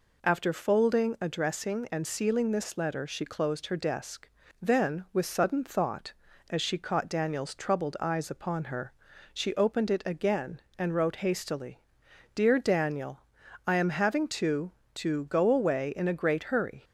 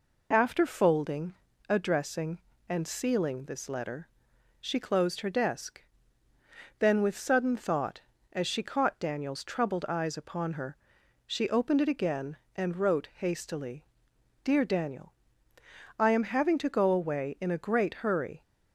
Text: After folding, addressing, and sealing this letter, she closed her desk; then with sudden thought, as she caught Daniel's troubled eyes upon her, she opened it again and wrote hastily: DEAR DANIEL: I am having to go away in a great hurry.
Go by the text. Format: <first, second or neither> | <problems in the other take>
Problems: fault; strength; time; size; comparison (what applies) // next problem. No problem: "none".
second | says "to" twice; at 14.9 s